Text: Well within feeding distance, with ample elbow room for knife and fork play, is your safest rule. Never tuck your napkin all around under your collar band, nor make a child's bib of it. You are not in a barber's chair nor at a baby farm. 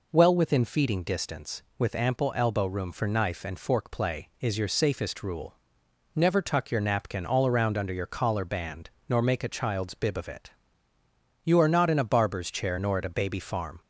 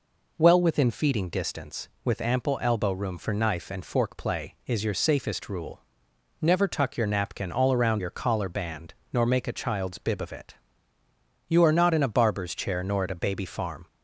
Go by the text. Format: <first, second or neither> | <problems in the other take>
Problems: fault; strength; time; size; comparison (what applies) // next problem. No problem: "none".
first | skips "under"; at 8.0 s